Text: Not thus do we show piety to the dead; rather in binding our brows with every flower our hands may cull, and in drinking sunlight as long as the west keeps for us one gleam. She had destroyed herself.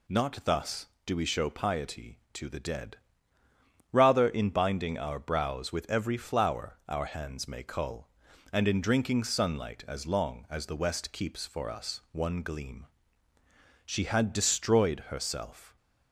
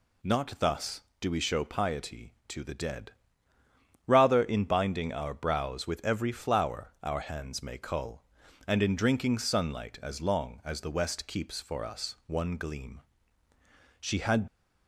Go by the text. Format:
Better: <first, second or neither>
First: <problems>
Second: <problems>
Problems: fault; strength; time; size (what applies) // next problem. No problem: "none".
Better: first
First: none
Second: stops before "destroyed herself"; at 14.4 s